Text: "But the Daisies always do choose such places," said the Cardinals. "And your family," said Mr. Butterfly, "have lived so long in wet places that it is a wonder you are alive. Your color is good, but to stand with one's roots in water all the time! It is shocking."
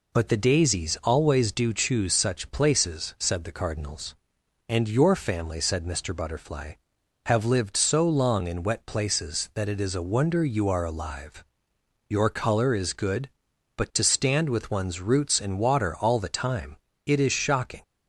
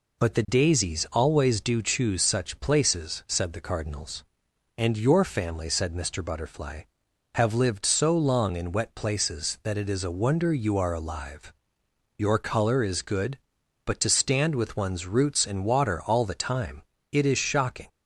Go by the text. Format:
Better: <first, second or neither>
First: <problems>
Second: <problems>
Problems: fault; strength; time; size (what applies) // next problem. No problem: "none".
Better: neither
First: none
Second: none